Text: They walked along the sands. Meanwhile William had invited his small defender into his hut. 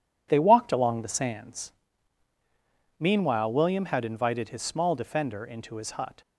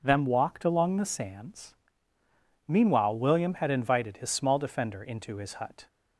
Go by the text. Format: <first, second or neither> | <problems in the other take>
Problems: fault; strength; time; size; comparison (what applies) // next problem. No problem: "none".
first | says "Them" for "They"; at 0.0 s